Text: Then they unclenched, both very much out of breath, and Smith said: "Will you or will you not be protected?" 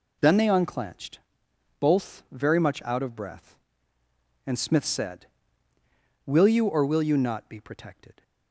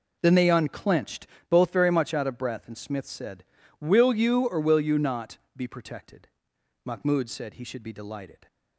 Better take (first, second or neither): first